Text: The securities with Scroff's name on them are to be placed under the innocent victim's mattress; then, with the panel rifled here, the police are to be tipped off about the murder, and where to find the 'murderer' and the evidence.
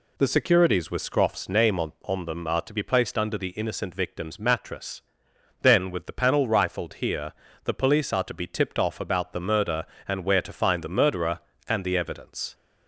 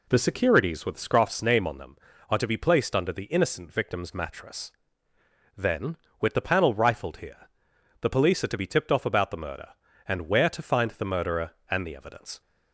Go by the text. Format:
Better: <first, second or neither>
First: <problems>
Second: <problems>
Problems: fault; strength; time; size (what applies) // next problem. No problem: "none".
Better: second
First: says "on" twice; at 2.0 s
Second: none